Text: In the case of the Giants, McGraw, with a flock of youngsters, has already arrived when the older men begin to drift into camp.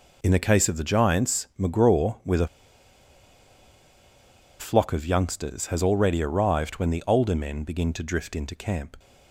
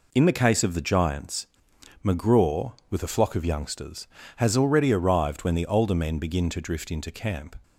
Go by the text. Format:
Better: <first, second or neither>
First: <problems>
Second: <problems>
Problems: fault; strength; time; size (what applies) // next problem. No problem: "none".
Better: second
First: pauses between "a" and "flock"; strong; at 2.4 s; 2.1 s long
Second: none